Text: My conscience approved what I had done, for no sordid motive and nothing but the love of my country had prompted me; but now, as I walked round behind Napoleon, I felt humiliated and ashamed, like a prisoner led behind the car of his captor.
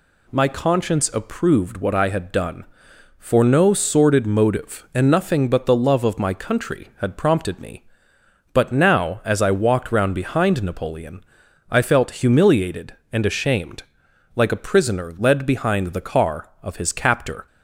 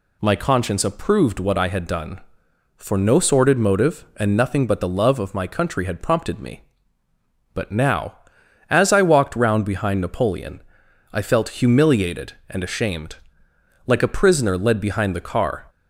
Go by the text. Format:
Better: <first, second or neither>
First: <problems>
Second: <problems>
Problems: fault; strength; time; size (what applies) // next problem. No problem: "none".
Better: first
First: none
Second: stops before "of his captor"; at 15.6 s